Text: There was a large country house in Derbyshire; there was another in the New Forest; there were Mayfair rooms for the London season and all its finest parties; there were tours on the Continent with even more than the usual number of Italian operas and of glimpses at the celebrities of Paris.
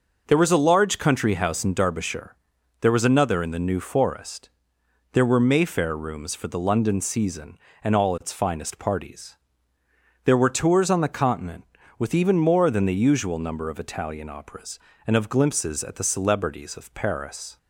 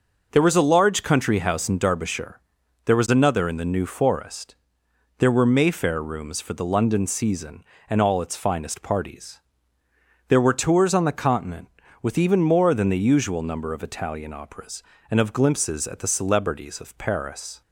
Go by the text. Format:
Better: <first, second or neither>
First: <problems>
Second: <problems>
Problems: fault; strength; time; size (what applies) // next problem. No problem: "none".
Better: neither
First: none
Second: none